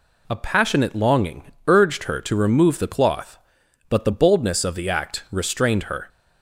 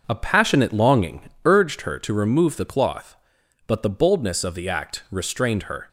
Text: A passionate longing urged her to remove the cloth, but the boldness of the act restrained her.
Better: first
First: pauses between "longing" and "urged"; slight; at 1.5 s; 0.16 s long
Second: starts louder than the rest; until 1.7 s; 6 dB // pauses between "longing" and "urged"; slight; at 1.2 s; 0.16 s long

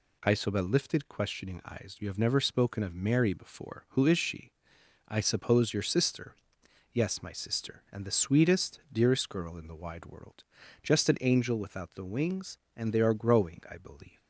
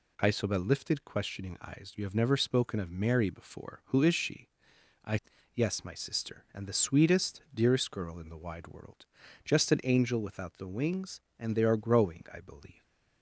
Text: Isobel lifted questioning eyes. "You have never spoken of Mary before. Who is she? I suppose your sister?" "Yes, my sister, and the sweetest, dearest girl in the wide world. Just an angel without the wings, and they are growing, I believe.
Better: first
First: none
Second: skips "suppose your sister"; at 5.3 s

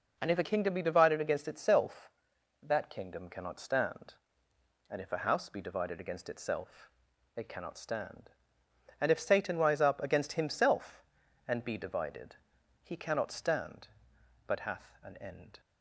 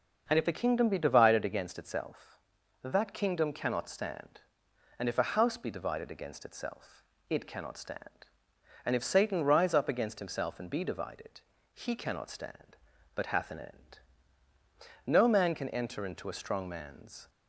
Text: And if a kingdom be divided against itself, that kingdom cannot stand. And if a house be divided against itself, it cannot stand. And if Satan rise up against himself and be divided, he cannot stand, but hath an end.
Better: first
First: none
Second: starts louder than the rest; noticeable; until 1.2 s; 6 dB // goes on to say "No man can enter into a strong man's"; strong; from 15.0 s on; 2.2 s long

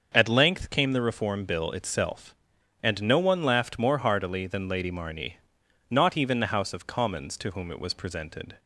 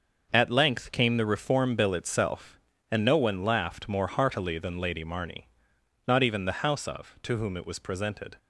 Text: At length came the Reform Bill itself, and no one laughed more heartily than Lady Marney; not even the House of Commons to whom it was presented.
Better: first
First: starts louder than the rest; until 1.1 s; 6.5 dB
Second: starts louder than the rest; until 1.3 s; 6.5 dB // skips "Commons"; at 7.2 s

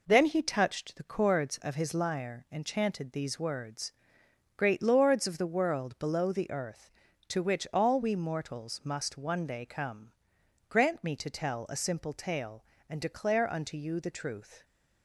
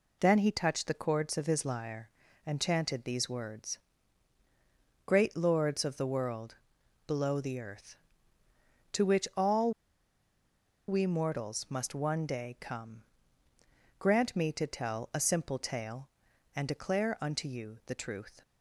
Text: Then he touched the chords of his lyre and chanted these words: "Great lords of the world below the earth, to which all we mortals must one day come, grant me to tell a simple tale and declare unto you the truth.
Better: first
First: none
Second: pauses between "world" and "below"; noticeable; at 6.5 s; 0.52 s long // pauses between "all" and "we"; at 9.7 s; 1.1 s long

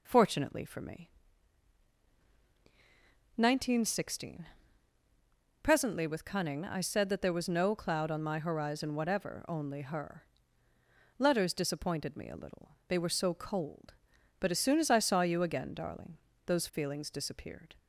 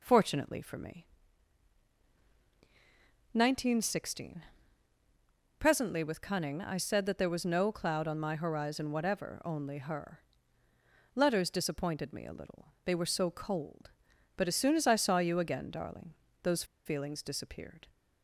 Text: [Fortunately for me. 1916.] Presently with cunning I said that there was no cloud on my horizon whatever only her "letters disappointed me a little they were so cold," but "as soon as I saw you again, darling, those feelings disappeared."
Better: first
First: pauses between "her" and "letters"; noticeable; at 10.2 s; 0.96 s long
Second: pauses between "her" and "letters"; noticeable; at 10.1 s; 0.96 s long // pauses between "those" and "feelings"; slight; at 16.6 s; 0.20 s long

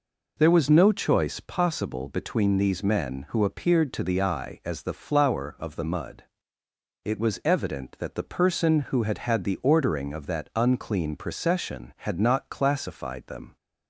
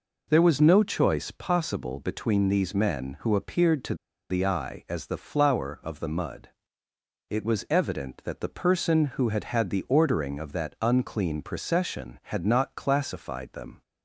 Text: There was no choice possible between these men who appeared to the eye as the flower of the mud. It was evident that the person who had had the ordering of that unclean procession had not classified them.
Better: first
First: none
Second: pauses between "to" and "the"; slight; at 3.9 s; 0.35 s long

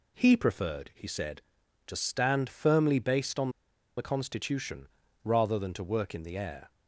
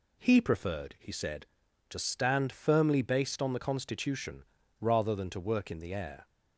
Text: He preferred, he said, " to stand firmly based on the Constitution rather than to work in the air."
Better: second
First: pauses between "on" and "the"; noticeable; at 3.4 s; 0.48 s long // pauses between "Constitution" and "rather"; slight; at 4.8 s; 0.36 s long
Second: pauses between "Constitution" and "rather"; slight; at 4.4 s; 0.36 s long

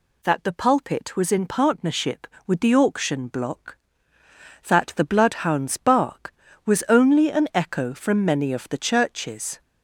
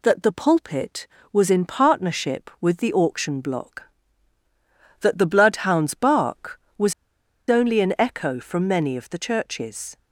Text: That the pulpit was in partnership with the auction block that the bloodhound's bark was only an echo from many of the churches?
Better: first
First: none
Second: pauses between "was" and "only"; noticeable; at 6.9 s; 0.56 s long

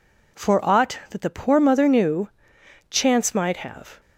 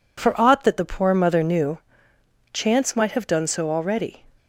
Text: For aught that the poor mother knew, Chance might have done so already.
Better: second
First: stops before "done so already"; at 3.9 s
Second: none

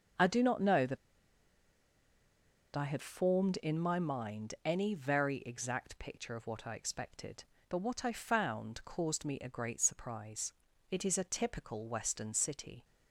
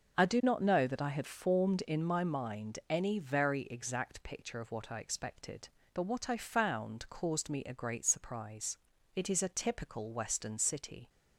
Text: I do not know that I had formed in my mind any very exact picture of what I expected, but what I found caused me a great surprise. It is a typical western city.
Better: second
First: pauses between "that" and "I"; strong; at 0.9 s; 1.7 s long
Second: none

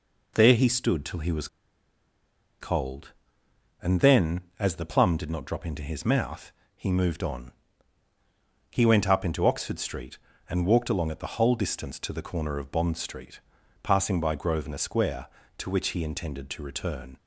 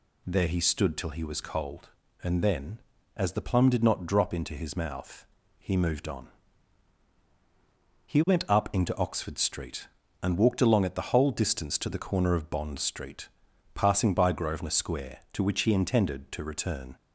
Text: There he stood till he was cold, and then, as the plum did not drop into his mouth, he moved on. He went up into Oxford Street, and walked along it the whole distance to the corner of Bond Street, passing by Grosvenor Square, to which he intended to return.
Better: second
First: pauses between "was" and "cold"; at 1.4 s; 1.1 s long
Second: none

